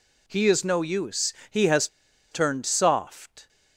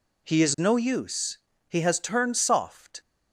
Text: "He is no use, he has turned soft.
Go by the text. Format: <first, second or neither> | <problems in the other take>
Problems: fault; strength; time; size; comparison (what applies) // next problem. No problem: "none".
second | pauses between "has" and "turned"; at 1.8 s; 0.44 s long